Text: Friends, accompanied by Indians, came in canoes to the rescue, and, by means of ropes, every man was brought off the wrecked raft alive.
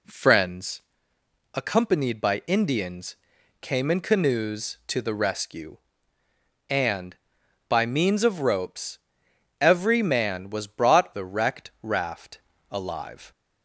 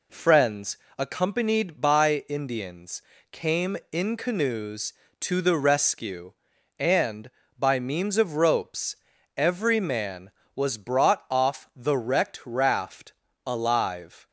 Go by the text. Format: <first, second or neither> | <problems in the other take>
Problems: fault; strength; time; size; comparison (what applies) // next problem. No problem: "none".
second | skips "off"; at 11.1 s // pauses between "raft" and "alive"; slight; at 12.3 s; 0.32 s long; slight in the second